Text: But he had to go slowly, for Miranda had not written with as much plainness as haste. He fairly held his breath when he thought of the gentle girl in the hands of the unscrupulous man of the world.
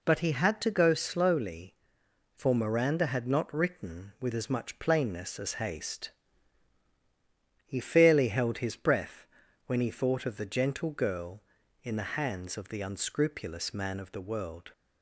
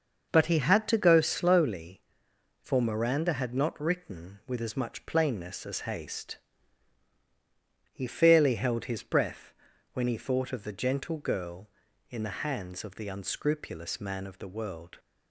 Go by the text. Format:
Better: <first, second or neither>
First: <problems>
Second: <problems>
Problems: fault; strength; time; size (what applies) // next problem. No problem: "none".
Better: first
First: pauses between "breath" and "when"; at 9.2 s; 0.42 s long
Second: starts louder than the rest; until 1.8 s; 6.5 dB // pauses between "breath" and "when"; at 9.5 s; 0.42 s long